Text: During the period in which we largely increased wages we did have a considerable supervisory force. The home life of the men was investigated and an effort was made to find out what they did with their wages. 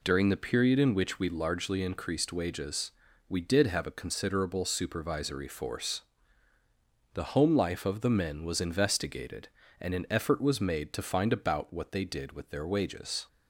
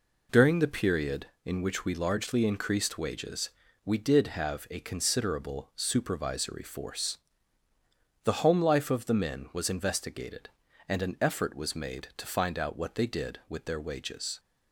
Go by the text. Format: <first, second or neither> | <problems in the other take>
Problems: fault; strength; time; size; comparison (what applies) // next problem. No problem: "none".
second | pauses between "wages" and "we"; at 2.9 s; 0.38 s long; slight in the second // says "about" for "out"; at 11.3 s